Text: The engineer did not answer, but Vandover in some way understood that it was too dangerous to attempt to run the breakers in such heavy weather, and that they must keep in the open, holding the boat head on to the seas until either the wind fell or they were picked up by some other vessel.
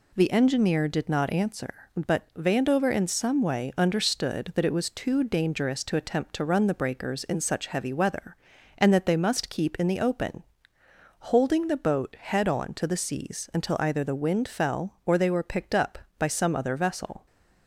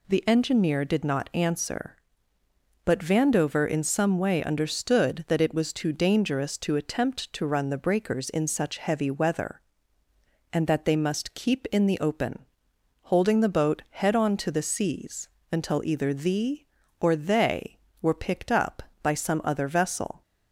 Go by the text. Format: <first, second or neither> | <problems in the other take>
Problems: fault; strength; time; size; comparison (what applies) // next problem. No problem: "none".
first | pauses between "seas" and "until"; slight; at 15.2 s; 0.24 s long // skips "wind fell"; at 16.8 s